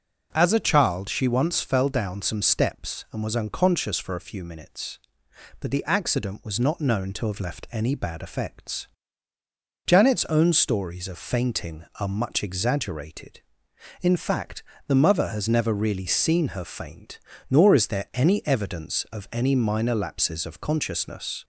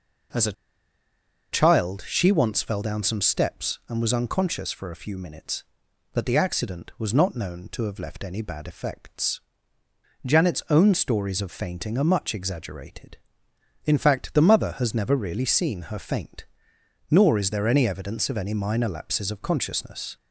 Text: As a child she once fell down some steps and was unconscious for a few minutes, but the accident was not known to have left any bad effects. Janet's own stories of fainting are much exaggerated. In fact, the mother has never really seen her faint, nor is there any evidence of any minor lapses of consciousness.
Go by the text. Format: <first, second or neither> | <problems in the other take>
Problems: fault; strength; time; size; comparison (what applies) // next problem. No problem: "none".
first | pauses between "a" and "child"; at 0.5 s; 0.98 s long